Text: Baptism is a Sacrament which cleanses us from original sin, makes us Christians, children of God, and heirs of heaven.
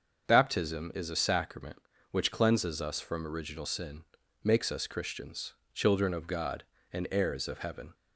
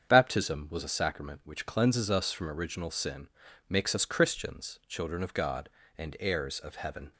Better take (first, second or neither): first